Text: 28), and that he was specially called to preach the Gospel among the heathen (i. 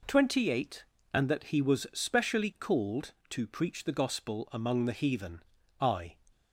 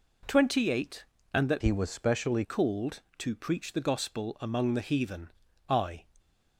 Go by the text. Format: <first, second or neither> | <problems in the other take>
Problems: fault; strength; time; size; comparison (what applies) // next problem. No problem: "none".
first | changes voice from "he" to "specially"; from 1.6 to 2.4 s; 0.8 s long